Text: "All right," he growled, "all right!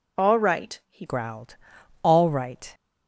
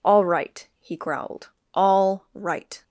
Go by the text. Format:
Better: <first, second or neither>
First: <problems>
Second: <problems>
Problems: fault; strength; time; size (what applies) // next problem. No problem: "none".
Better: second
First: changes voice at "growled"; from 1.0 s on; 1.7 s long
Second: none